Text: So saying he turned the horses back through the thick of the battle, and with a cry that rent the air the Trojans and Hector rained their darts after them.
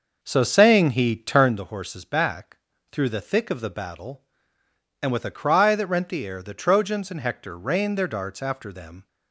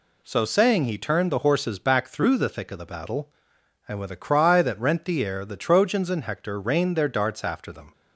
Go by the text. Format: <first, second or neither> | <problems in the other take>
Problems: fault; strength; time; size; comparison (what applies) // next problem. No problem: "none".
second | starts louder than the rest; noticeable; until 1.6 s; 6 dB // pauses between "back" and "through"; slight; at 2.5 s; 0.34 s long